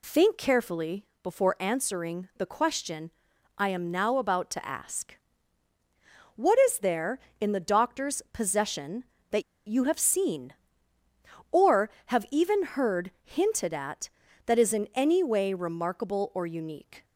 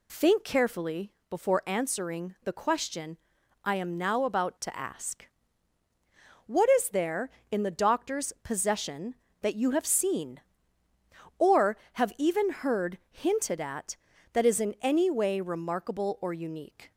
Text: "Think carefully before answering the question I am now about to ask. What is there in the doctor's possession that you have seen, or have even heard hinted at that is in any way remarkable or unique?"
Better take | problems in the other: second | pauses between "carefully" and "before"; slight; at 1.0 s; 0.16 s long; slight in the second // pauses between "question" and "I"; noticeable; at 3.1 s; 0.46 s long; noticeable in the second // pauses between "that" and "you"; slight; at 9.4 s; 0.25 s long

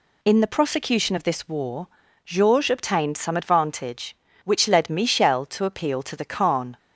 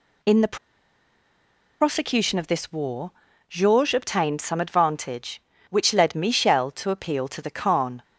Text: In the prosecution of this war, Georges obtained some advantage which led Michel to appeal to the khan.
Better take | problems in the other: first | pauses between "the" and "prosecution"; strong; at 0.5 s; 1.2 s long

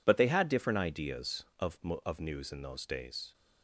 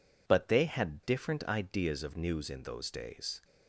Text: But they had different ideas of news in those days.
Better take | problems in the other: second | says "of" twice; at 2.0 s

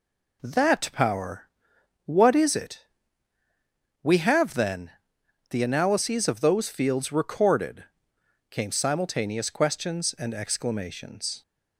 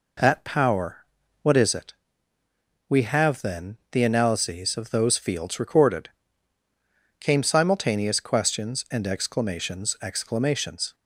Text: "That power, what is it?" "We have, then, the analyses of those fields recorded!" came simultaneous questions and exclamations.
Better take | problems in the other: first | says "exclamations" twice; at 10.0 s

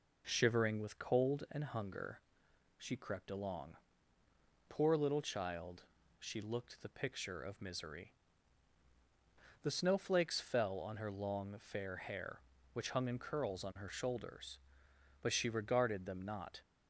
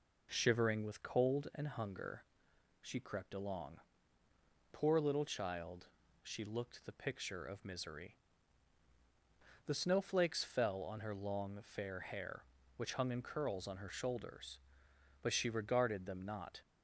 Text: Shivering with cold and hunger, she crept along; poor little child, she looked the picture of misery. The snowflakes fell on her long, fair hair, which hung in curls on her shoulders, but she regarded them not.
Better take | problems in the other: neither | none

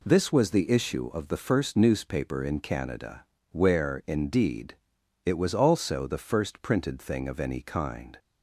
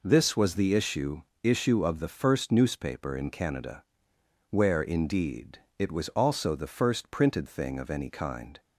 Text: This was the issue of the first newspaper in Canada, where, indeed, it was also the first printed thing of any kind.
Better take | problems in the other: first | says "issue" twice; at 1.4 s

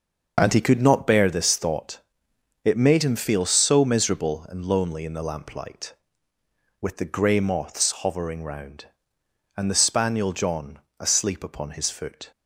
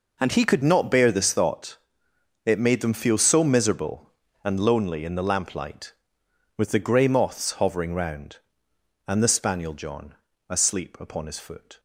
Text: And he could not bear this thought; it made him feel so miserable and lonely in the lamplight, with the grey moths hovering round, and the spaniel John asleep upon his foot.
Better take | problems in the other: first | says "them" for "him"; at 2.7 s // pauses between "John" and "asleep"; slight; at 10.1 s; 0.34 s long; slight in the first

